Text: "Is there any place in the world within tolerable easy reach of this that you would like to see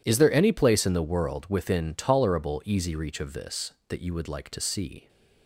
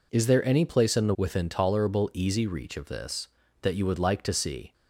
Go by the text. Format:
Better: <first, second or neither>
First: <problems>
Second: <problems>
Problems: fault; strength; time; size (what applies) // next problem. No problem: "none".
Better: first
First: none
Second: skips "world"; at 1.1 s